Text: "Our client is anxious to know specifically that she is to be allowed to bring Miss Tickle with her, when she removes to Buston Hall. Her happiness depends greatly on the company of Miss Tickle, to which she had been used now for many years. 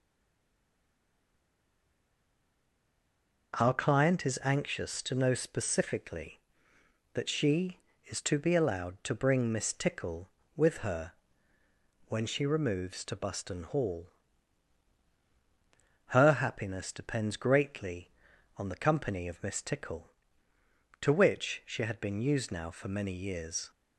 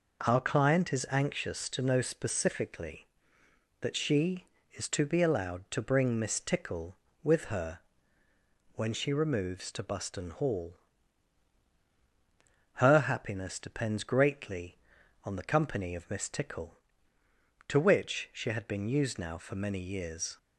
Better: second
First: stays silent before the first word; strong; until 3.5 s; 3.5 s long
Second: none

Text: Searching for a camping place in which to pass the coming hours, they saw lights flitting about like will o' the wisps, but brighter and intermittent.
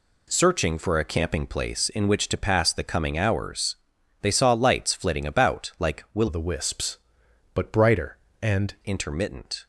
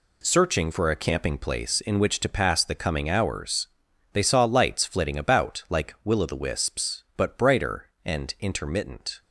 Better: second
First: changes voice from "o" to "and"; from 6.2 to 8.7 s; 2.5 s long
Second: none

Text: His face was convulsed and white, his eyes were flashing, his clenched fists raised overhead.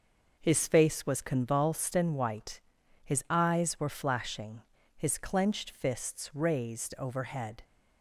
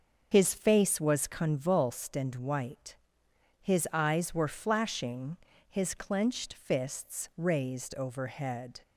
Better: first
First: none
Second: loses the start of "His"; at 0.3 s; 35 ms // starts louder than the rest; until 1.3 s; 6 dB

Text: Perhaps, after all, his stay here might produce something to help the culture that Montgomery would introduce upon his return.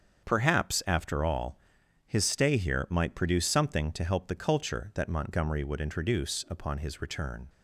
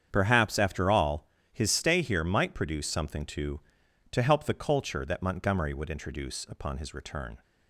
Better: first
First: starts louder than the rest; strong; until 1.2 s; 7 dB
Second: starts louder than the rest; strong; until 1.1 s; 8 dB // says "to" twice; at 4.1 s

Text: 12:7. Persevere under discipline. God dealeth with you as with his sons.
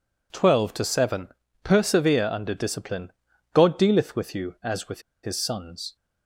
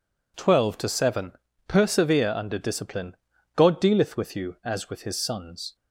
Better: second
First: pauses between "with" and "his"; slight; at 5.0 s; 0.23 s long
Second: none

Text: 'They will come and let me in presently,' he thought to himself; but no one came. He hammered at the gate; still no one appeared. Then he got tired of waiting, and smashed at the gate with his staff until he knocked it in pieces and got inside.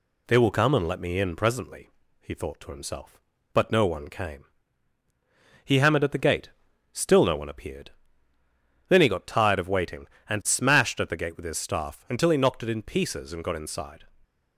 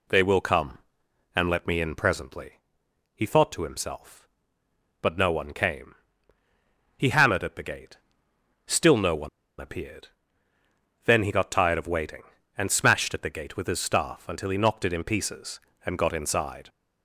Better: first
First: none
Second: pauses between "one" and "appeared"; slight; at 9.2 s; 0.31 s long

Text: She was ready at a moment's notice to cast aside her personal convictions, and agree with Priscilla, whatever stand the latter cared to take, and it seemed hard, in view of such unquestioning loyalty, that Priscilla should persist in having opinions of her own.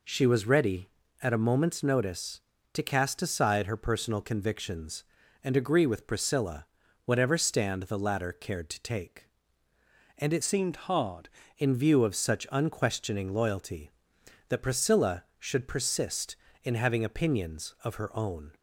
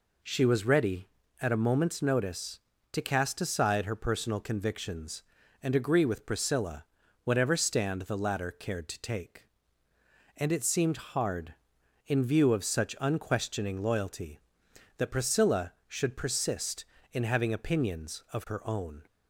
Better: second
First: changes voice from "seemed" to "hard"; from 10.4 to 11.2 s; 0.8 s long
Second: none

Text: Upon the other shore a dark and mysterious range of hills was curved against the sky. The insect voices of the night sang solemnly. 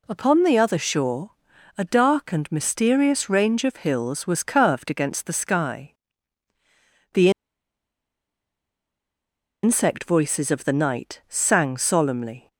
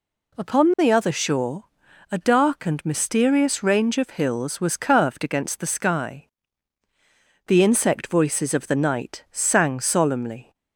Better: second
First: pauses between "shore" and "a"; noticeable; at 1.2 s; 0.48 s long // pauses between "The" and "insect"; strong; at 7.2 s; 2.3 s long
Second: pauses between "shore" and "a"; noticeable; at 1.6 s; 0.48 s long

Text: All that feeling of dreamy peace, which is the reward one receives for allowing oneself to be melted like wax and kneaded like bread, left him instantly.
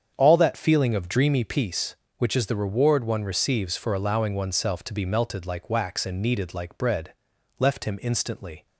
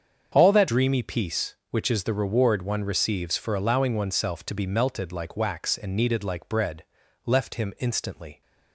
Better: first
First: starts louder than the rest; strong; until 1.1 s; 7.5 dB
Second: starts louder than the rest; strong; until 1.3 s; 7 dB // skips "feeling of"; at 0.6 s

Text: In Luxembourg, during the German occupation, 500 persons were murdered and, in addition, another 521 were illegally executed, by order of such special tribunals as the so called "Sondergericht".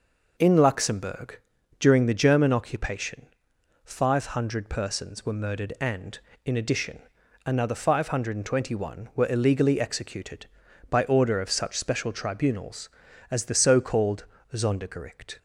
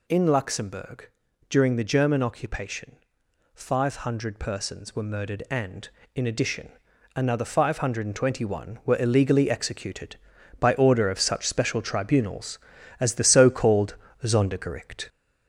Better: first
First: pauses between "called" and "Sondergericht"; slight; at 14.2 s; 0.26 s long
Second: gets louder; throughout; 4 dB // pauses between "called" and "Sondergericht"; slight; at 13.9 s; 0.26 s long

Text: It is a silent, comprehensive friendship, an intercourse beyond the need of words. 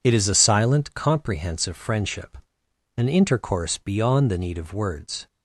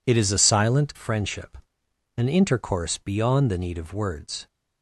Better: first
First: none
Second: skips "comprehensive"; at 0.9 s

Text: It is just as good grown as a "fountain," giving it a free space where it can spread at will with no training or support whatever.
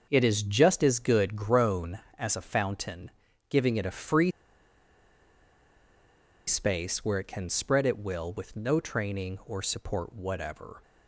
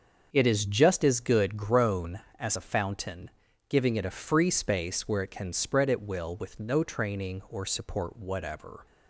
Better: second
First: starts louder than the rest; until 1.1 s; 6.5 dB // pauses between "free" and "space"; strong; at 4.2 s; 2.1 s long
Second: starts louder than the rest; until 1.3 s; 6.5 dB

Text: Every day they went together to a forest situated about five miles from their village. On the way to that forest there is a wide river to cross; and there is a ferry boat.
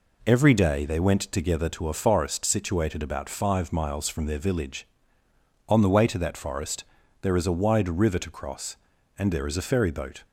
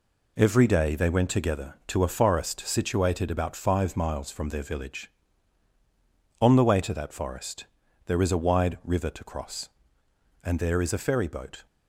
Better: neither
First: pauses between "forest" and "there"; at 6.8 s; 0.38 s long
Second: pauses between "forest" and "there"; at 7.6 s; 0.40 s long

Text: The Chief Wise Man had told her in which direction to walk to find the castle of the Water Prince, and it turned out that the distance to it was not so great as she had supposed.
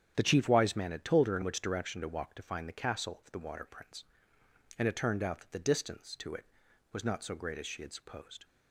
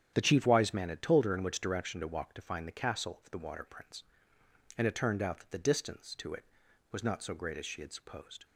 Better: neither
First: starts louder than the rest; strong; until 1.1 s; 9 dB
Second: starts louder than the rest; strong; until 1.1 s; 9.5 dB

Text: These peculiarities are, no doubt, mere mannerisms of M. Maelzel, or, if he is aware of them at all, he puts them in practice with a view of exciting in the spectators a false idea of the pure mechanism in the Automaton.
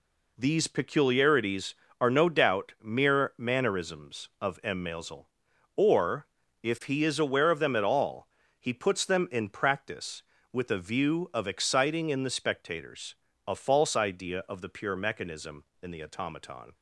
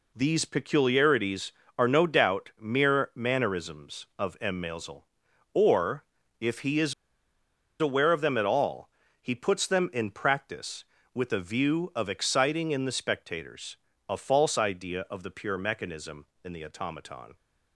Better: first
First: pauses between "spectators" and "a"; slight; at 13.1 s; 0.32 s long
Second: pauses between "is" and "aware"; noticeable; at 6.9 s; 0.86 s long // pauses between "spectators" and "a"; slight; at 13.7 s; 0.32 s long

